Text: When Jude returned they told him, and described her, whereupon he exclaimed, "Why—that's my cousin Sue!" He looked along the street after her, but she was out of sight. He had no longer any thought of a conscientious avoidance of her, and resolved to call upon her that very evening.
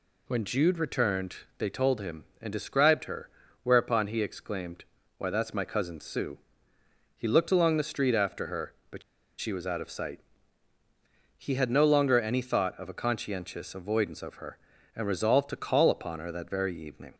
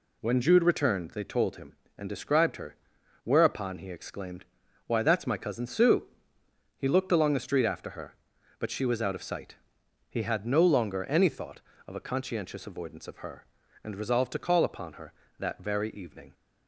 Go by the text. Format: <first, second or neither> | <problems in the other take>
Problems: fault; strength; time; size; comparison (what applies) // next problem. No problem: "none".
second | pauses between "returned" and "they"; slight; at 1.3 s; 0.22 s long // pauses between "but" and "she"; at 9.0 s; 0.38 s long